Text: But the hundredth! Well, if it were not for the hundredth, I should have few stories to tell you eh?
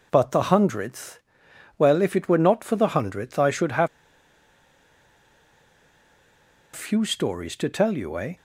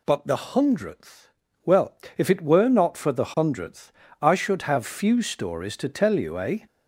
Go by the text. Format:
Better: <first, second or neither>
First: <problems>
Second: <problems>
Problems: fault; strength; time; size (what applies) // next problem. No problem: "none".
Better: second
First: pauses between "have" and "few"; strong; at 3.8 s; 2.8 s long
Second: none